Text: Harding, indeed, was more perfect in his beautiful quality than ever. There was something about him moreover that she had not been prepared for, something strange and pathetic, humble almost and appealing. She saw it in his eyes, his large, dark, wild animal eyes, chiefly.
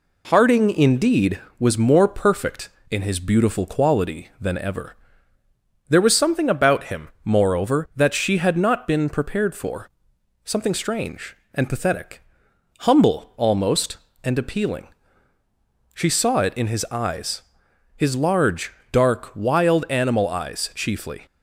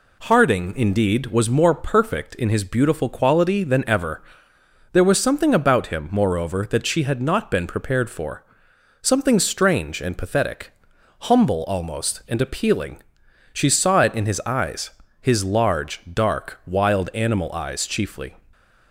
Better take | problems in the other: neither | none

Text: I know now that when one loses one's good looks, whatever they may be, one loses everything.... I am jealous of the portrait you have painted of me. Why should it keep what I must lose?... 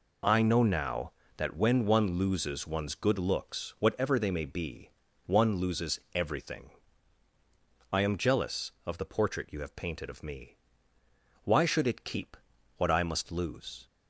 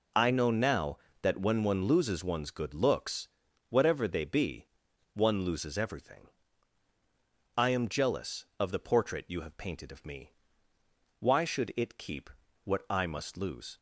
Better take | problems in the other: first | skips "may"; at 4.2 s // pauses between "keep" and "what"; slight; at 12.3 s; 0.32 s long; also in the first

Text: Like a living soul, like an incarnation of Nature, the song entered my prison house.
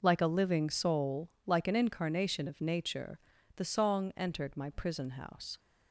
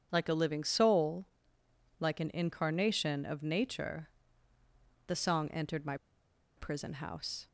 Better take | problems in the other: first | pauses between "my" and "prison"; noticeable; at 5.9 s; 0.60 s long

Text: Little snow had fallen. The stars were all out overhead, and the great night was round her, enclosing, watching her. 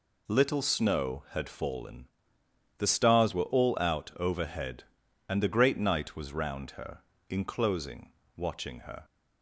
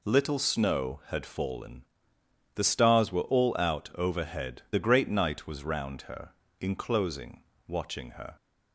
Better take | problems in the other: first | skips "and"; at 4.6 s

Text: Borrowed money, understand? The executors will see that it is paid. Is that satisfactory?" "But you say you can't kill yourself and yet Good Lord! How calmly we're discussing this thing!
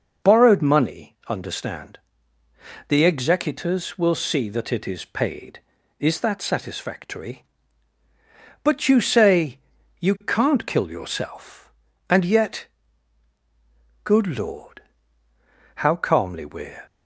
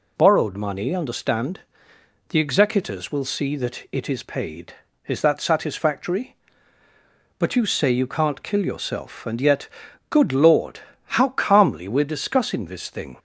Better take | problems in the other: second | pauses between "say" and "you"; at 9.5 s; 0.42 s long // pauses between "yet" and "Good"; strong; at 12.6 s; 1.3 s long; also in the second // stops before "discussing this thing"; at 16.8 s

